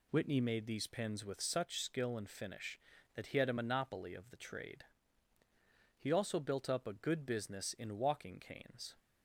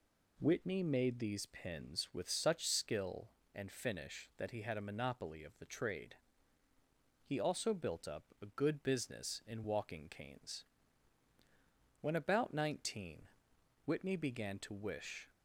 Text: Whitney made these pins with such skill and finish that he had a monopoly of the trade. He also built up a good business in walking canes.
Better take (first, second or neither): first